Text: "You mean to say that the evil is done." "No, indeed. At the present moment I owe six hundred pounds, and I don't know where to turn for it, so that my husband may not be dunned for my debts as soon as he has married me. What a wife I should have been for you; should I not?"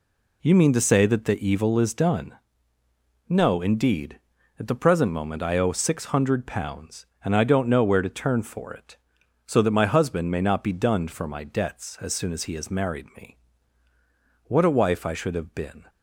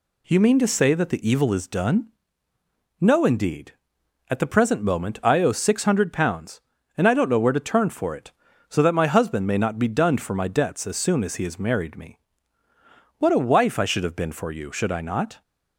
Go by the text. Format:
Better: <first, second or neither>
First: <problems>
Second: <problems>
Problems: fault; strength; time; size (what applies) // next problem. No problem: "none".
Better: second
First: stops before "for you should I not"; at 15.8 s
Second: none